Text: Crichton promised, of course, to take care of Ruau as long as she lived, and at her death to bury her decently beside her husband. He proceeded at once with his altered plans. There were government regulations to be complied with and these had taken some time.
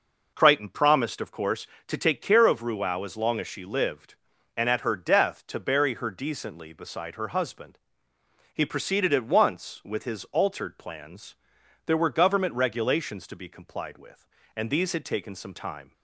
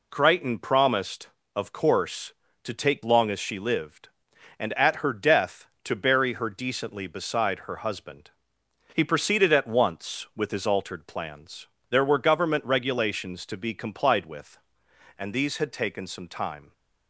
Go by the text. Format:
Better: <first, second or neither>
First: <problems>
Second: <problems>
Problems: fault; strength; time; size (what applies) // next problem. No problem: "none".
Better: first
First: none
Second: skips "care of Ruau as"; at 3.0 s